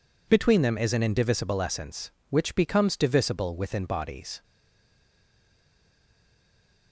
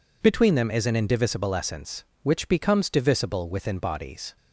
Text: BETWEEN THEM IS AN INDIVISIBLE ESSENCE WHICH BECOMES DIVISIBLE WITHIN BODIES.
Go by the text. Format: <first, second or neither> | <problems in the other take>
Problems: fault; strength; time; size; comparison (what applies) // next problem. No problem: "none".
second | stays silent after the last word; from 4.4 s on; 2.5 s long